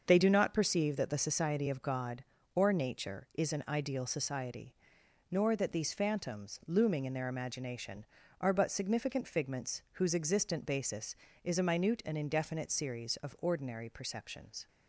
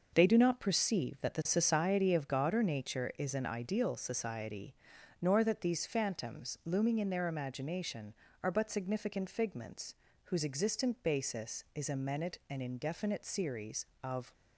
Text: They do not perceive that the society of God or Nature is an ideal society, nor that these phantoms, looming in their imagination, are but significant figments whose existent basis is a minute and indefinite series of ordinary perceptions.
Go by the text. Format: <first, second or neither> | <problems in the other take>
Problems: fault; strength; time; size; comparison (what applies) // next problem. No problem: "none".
first | starts louder than the rest; noticeable; until 1.1 s; 6 dB; also in the first // pauses between "figments" and "whose"; slight; at 9.9 s; 0.30 s long // stops before "ordinary perceptions"; at 14.3 s